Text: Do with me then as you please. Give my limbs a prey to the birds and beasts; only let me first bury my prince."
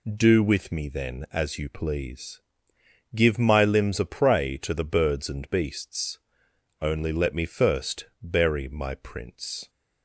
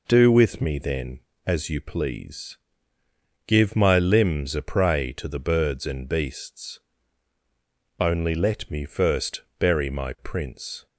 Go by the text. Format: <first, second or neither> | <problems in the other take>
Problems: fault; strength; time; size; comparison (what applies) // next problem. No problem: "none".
neither | pauses between "first" and "bury"; slight; the same in both